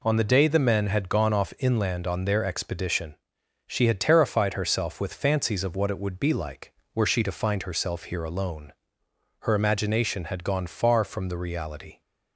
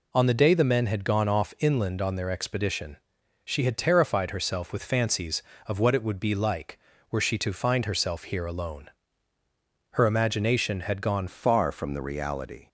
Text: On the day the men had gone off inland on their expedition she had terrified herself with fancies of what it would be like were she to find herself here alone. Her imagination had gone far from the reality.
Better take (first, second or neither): first